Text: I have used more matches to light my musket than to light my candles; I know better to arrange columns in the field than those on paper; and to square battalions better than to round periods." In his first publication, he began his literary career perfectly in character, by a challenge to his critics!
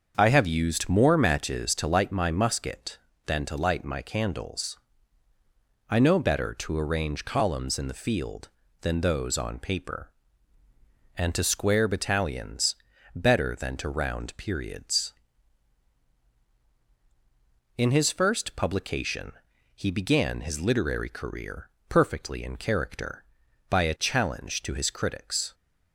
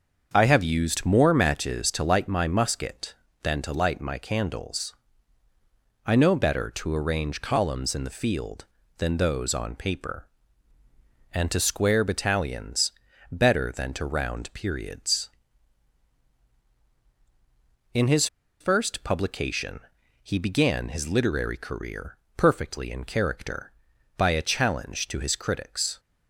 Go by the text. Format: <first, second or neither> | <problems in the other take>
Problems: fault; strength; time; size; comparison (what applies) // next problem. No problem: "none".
first | starts louder than the rest; until 1.3 s; 7 dB; also in the first // pauses between "battalions" and "better"; at 12.9 s; 0.38 s long; also in the first // pauses between "his" and "first"; slight; at 18.2 s; 0.34 s long // pauses between "career" and "perfectly"; slight; at 22.1 s; 0.22 s long; slight in the first